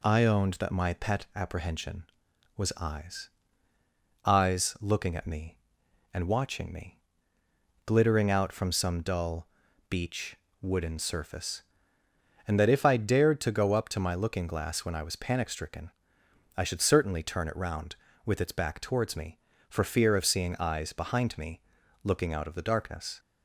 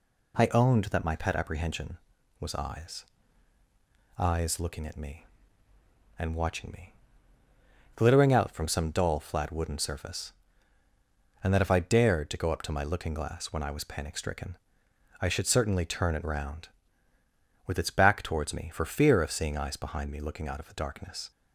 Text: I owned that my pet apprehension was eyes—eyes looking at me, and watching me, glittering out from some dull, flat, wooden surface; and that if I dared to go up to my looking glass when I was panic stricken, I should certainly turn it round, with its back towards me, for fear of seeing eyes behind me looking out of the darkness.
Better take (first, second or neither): second